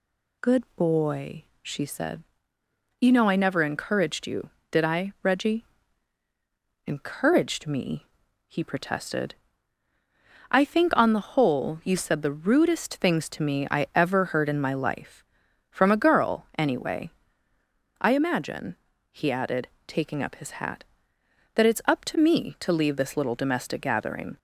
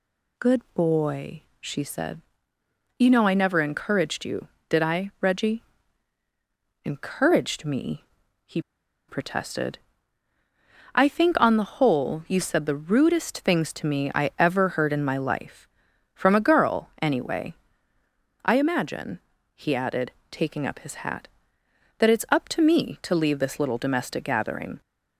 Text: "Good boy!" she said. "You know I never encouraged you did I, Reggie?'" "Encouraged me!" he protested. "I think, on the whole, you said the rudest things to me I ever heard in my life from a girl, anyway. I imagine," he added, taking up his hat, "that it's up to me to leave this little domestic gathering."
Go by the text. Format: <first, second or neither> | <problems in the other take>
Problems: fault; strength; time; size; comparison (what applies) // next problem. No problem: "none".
first | pauses between "he" and "protested"; noticeable; at 8.6 s; 0.47 s long